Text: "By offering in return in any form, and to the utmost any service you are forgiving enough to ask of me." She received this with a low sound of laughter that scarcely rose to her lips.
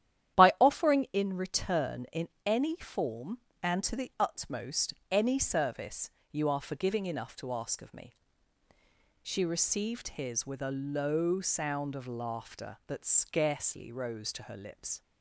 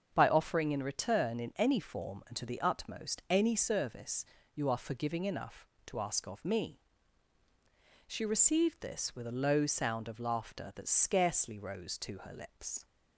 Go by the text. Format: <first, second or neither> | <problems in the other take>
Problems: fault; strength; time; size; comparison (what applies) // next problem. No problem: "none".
second | starts louder than the rest; strong; until 1.4 s; 11 dB; also in the second // pauses between "in" and "any"; slight; at 2.2 s; 0.18 s long // pauses between "utmost" and "any"; slight; at 4.9 s; 0.16 s long // pauses between "service" and "you"; slight; at 6.1 s; 0.22 s long; slight in the second // says "his" for "this"; at 10.1 s